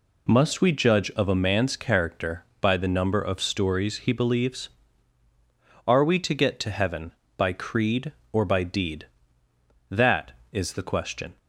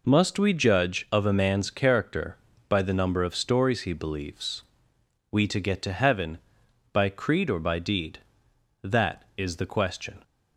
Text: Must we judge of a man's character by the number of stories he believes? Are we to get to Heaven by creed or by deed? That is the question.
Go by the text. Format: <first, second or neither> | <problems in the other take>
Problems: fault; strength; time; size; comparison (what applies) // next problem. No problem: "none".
first | skips "Are"; at 4.9 s